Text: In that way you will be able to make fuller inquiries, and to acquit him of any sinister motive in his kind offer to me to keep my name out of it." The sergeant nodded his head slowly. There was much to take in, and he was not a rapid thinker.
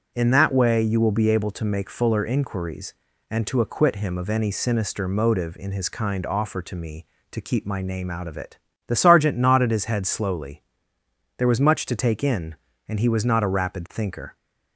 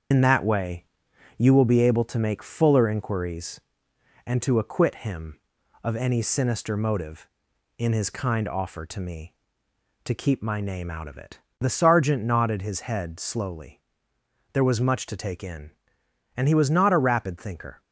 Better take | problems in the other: first | loses the start of "In"; at 0.1 s; 90 ms // starts louder than the rest; strong; until 1.6 s; 7.5 dB; strong in the first // pauses between "way" and "you"; noticeable; at 0.8 s; 0.52 s long

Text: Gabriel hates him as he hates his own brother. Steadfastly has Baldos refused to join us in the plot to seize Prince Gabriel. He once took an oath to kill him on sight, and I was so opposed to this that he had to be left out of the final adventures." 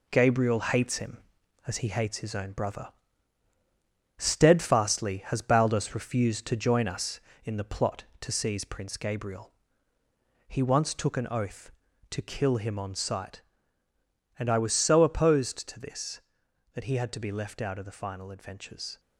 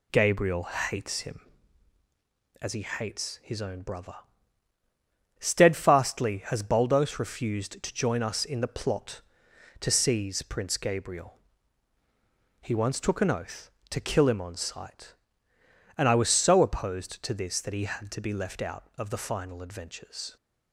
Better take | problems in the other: second | gets quieter; throughout; 7 dB

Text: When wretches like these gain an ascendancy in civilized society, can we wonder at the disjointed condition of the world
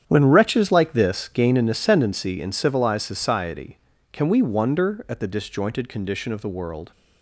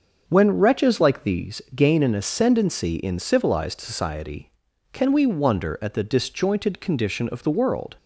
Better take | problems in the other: second | starts louder than the rest; strong; until 1.0 s; 9 dB; also in the second // says "this" for "these"; at 0.9 s

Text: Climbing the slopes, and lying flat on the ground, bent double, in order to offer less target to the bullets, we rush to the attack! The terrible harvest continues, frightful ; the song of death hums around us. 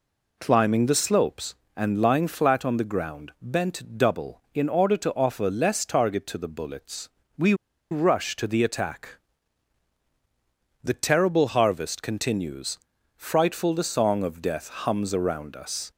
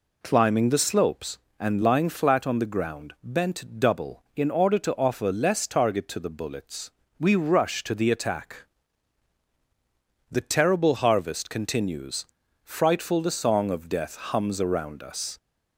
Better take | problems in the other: second | pauses between "we" and "rush"; at 7.5 s; 0.37 s long

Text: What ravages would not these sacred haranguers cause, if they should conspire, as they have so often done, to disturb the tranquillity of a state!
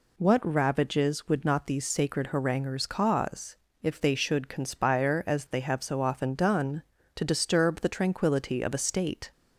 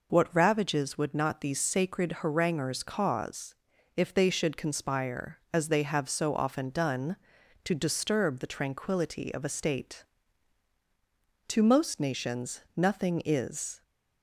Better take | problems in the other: first | goes on to say "To most nations nothing is"; strong; from 11.4 s on; 2.3 s long

